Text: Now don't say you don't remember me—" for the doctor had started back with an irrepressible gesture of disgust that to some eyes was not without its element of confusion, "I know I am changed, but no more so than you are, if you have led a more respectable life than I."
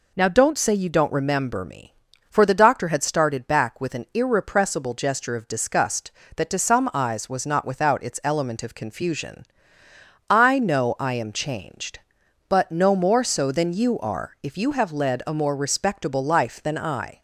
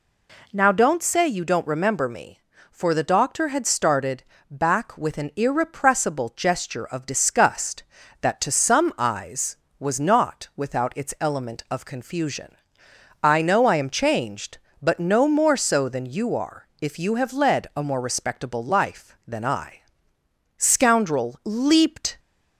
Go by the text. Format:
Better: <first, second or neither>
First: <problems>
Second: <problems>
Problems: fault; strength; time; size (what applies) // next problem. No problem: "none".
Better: first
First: none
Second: pauses between "started" and "back"; slight; at 4.2 s; 0.26 s long // goes on to say "Scoundrel leaped"; from 20.5 s on; 1.6 s long